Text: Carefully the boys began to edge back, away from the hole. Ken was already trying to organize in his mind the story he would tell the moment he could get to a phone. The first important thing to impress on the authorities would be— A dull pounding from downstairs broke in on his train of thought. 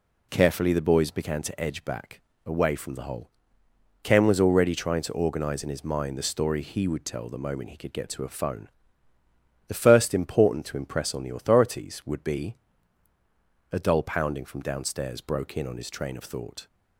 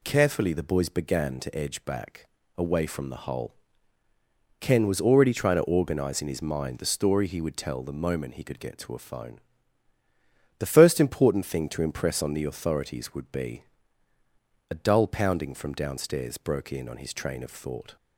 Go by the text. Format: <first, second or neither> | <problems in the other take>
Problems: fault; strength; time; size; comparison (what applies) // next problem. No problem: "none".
second | skips "thing"; at 10.6 s